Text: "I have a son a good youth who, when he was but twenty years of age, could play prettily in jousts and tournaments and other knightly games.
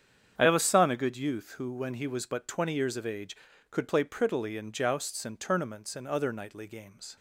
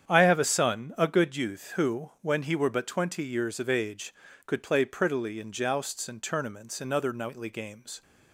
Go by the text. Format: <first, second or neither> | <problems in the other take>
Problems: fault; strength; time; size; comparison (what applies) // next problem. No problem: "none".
first | starts louder than the rest; strong; until 1.1 s; 8.5 dB; strong in the first // says "were" for "was"; at 2.5 s